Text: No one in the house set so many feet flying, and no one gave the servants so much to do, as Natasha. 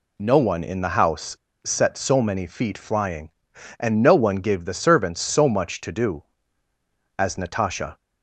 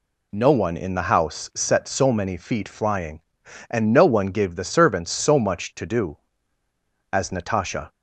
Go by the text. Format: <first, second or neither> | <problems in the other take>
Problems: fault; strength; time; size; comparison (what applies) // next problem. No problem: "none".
second | pauses between "house" and "set"; slight; at 1.3 s; 0.26 s long